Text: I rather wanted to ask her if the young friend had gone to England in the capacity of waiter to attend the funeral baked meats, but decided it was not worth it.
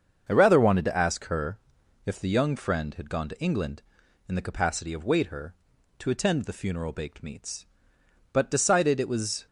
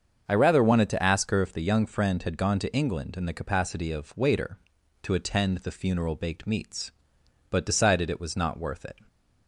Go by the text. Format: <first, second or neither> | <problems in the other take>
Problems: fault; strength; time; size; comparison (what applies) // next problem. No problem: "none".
second | starts louder than the rest; until 1.2 s; 7 dB; also in the second // pauses between "her" and "if"; noticeable; at 1.5 s; 0.46 s long // stops before "not worth it"; at 9.4 s